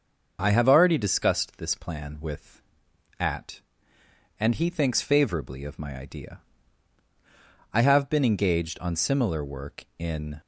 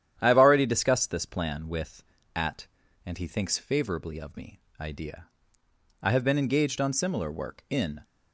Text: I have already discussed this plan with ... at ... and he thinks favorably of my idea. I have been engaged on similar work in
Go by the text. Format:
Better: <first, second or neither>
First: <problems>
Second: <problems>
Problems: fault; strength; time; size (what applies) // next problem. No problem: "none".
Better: first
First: starts louder than the rest; until 1.4 s; 6.5 dB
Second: starts louder than the rest; strong; until 1.2 s; 10 dB // says "me" for "my"; at 4.3 s